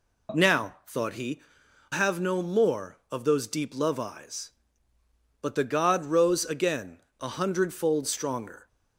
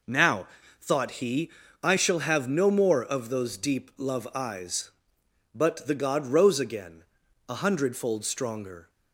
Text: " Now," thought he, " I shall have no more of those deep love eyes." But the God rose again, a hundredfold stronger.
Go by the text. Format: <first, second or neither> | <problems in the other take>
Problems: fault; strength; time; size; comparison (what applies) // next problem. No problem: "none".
second | skips "I shall"; at 1.9 s